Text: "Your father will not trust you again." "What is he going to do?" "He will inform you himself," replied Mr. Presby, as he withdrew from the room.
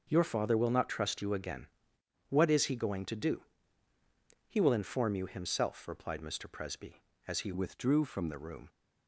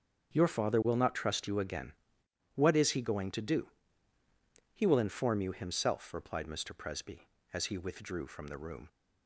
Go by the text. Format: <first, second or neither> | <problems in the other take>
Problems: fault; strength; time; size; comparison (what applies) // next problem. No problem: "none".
second | starts louder than the rest; until 1.1 s; 6.5 dB; strong in the second // changes voice from "withdrew" to "from"; from 7.5 to 8.2 s; 0.7 s long